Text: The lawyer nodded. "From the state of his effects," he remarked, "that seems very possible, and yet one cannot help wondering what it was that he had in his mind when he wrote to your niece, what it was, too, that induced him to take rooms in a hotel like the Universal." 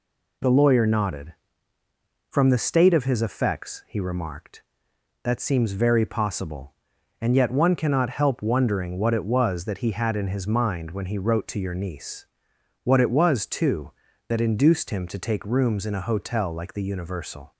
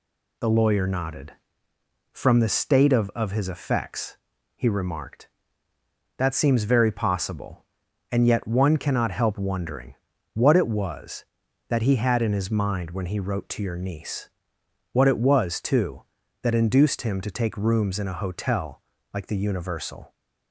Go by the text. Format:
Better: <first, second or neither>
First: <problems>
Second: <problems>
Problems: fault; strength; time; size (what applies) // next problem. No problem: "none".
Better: first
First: none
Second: says "of" twice; at 3.1 s // pauses between "wondering" and "what"; at 9.9 s; 0.40 s long // pauses between "hotel" and "like"; slight; at 18.8 s; 0.32 s long